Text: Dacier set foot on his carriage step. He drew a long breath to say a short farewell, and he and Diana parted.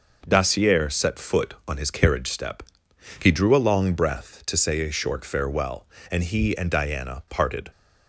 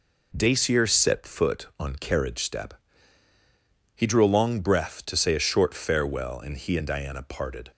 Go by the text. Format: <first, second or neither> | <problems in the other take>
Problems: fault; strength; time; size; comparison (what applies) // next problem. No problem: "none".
first | skips "his"; at 1.9 s